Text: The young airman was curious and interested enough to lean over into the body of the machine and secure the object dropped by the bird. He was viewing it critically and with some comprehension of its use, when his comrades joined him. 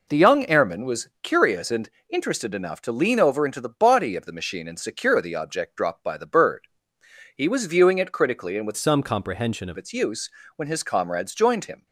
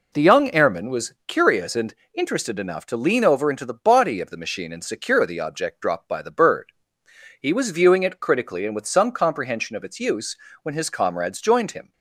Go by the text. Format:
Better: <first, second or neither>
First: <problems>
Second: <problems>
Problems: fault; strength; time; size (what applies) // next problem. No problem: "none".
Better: second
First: pauses between "and" and "interested"; slight; at 1.8 s; 0.18 s long // changes voice from "some" to "of"; from 8.7 to 9.7 s; 1.0 s long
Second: pauses between "and" and "interested"; slight; at 1.9 s; 0.18 s long